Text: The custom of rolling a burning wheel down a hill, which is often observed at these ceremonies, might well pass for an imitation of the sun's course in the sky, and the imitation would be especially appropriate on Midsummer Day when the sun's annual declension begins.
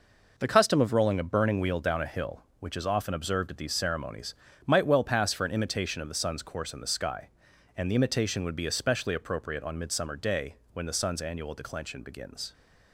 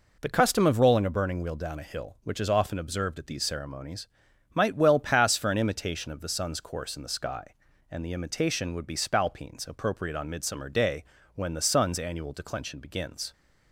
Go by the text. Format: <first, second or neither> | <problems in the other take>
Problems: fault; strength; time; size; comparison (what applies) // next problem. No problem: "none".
first | says "spalpeens" for "especially"; at 8.9 s // pauses between "Day" and "when"; slight; at 11.0 s; 0.32 s long; slight in the first